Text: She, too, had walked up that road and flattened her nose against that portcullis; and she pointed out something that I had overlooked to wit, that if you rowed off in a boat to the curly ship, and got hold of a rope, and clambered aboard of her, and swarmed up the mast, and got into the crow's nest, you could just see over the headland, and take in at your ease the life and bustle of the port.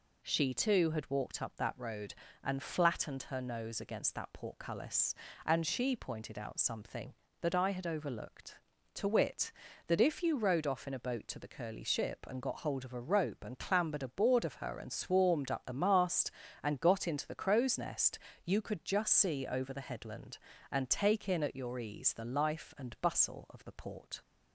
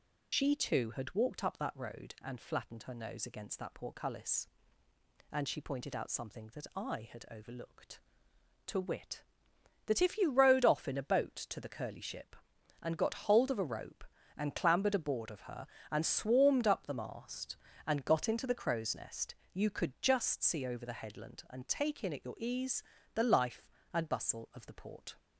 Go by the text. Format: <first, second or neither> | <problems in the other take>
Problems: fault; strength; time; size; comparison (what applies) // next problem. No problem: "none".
first | loses the start of "She"; at 0.3 s; 110 ms // pauses between "ease" and "the"; slight; at 22.8 s; 0.32 s long